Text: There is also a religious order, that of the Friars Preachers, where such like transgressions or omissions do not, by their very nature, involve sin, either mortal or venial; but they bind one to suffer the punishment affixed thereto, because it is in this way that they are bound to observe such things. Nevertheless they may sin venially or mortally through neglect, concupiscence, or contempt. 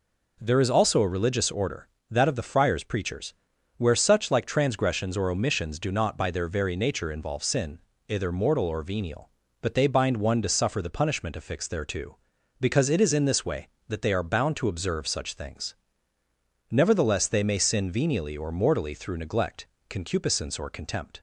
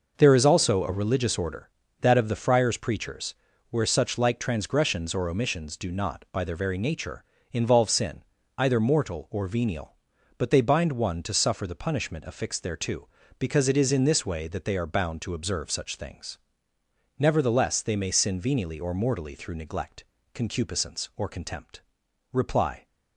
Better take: first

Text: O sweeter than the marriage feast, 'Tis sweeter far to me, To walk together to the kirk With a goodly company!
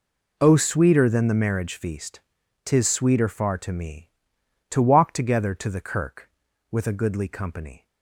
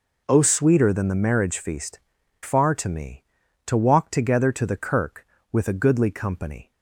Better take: first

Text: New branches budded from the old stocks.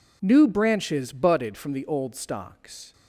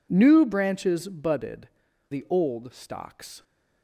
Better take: first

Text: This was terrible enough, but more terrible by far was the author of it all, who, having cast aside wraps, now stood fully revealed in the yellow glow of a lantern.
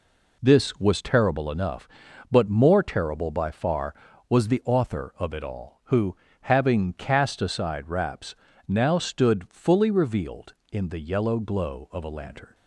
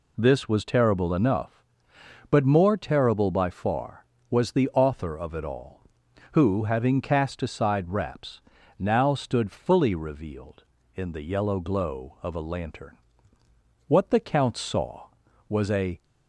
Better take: first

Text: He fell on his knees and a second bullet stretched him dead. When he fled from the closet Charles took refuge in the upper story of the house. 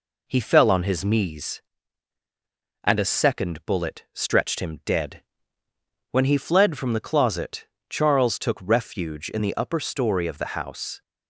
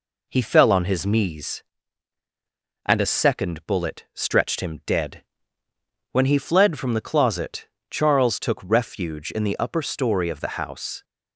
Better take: neither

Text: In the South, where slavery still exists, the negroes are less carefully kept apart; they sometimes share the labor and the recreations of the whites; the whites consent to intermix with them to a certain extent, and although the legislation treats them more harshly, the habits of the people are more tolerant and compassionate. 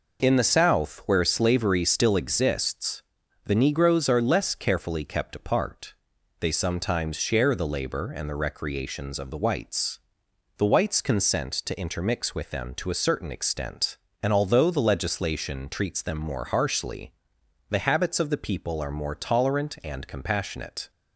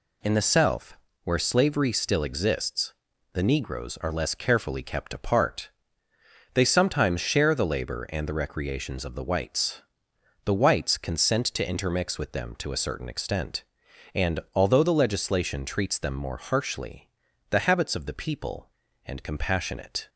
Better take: first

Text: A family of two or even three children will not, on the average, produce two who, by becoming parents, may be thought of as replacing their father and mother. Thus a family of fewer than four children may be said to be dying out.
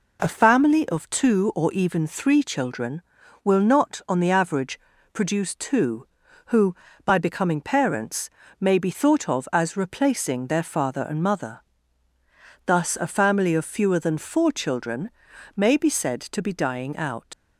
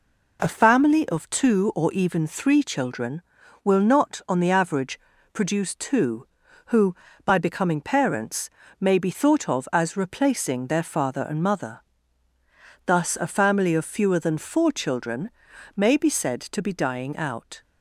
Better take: second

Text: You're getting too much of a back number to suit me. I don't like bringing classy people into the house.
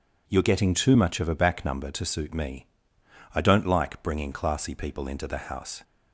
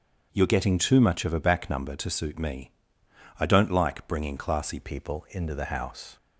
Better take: first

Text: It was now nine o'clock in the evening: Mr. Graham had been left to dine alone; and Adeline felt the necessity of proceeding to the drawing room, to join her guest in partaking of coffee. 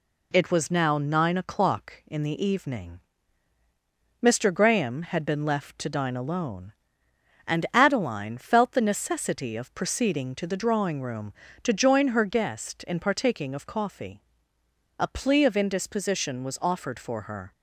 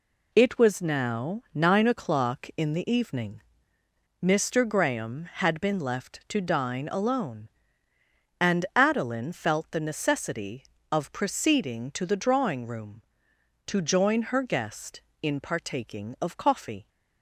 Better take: second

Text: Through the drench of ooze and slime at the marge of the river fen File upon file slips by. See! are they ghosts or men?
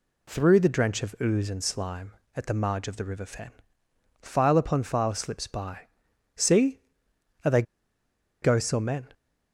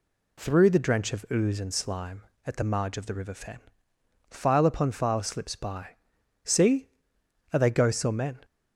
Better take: second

